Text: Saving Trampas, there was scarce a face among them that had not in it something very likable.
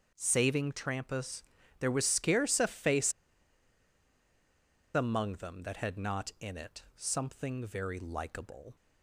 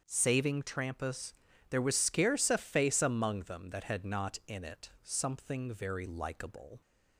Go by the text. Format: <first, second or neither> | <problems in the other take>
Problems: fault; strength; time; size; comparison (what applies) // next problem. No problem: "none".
second | starts louder than the rest; until 1.1 s; 7 dB; also in the second // pauses between "face" and "among"; strong; at 3.1 s; 1.8 s long